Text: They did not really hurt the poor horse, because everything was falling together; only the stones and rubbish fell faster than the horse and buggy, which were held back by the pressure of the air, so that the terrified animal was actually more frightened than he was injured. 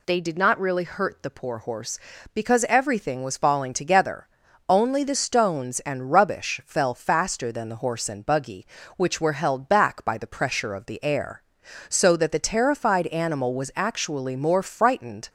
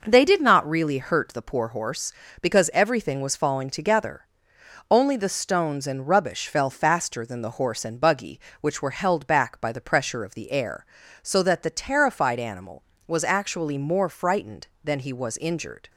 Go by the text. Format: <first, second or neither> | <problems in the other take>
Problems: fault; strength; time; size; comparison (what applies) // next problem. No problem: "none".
second | stops before "than he was injured"; at 15.2 s